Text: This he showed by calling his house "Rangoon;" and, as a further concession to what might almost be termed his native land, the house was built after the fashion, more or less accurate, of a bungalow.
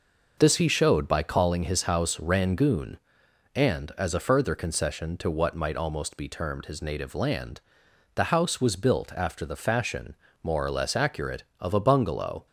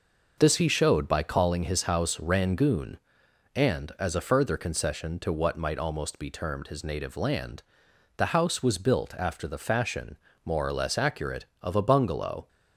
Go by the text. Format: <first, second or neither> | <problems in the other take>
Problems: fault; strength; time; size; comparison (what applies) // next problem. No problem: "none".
neither | none